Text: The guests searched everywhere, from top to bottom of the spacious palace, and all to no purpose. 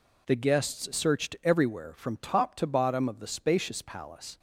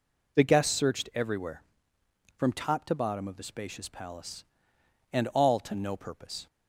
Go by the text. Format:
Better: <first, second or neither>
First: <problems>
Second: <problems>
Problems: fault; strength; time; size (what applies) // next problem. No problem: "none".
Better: second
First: stops before "and all to no purpose"; at 4.3 s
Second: none